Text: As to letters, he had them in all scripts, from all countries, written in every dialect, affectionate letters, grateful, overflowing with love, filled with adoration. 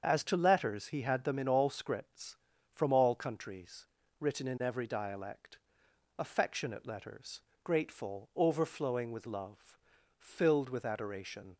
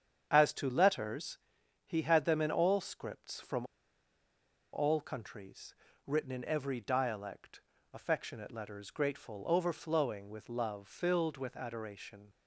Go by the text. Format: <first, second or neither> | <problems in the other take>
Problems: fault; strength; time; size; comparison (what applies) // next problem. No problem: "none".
first | starts louder than the rest; strong; until 1.3 s; 8 dB; also in the first // pauses between "from" and "all"; at 3.6 s; 1.0 s long